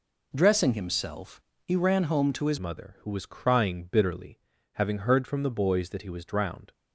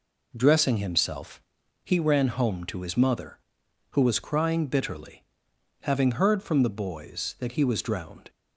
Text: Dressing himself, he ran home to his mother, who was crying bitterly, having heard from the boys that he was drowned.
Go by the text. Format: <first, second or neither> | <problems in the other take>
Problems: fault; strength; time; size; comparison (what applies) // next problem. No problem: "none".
second | changes voice at "mother"; from 2.5 s on; 4.2 s long